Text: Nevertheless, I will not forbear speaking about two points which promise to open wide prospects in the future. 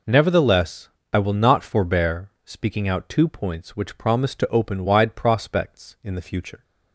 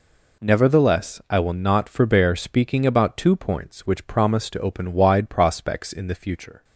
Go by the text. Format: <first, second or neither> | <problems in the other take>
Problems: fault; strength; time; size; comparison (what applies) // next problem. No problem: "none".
second | says "out" for "about"; at 2.8 s